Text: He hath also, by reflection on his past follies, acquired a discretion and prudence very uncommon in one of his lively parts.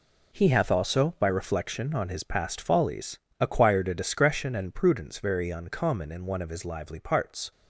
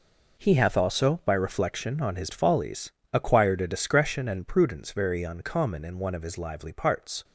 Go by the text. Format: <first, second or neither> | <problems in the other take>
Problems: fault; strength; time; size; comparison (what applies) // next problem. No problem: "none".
first | skips "past"; at 2.3 s